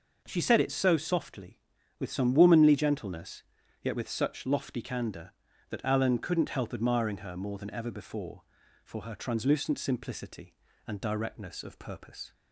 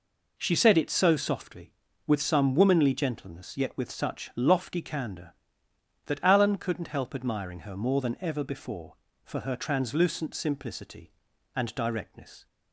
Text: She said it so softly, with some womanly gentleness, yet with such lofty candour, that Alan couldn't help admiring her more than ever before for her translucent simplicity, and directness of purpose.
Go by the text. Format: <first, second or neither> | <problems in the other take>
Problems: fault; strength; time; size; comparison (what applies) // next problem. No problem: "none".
first | stops before "of purpose"; at 12.4 s